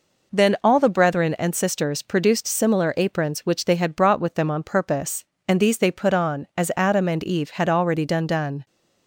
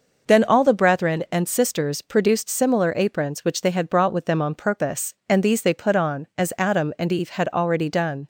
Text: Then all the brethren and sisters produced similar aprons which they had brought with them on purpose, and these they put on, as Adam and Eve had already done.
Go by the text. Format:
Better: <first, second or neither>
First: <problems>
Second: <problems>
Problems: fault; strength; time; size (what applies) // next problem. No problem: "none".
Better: second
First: says "done" twice; at 8.2 s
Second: none